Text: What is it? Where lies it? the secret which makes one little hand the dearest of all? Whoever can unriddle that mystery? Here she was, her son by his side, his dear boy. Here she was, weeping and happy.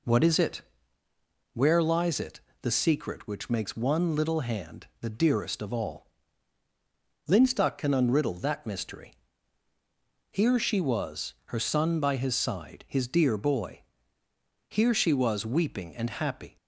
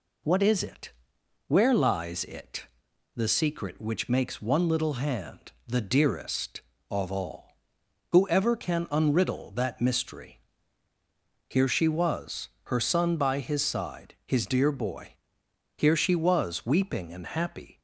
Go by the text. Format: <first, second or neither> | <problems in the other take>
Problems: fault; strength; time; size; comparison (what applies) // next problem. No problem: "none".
second | pauses between "hand" and "the"; slight; at 4.8 s; 0.16 s long; slight in the second // says "Linstock" for "Whoever"; at 7.2 s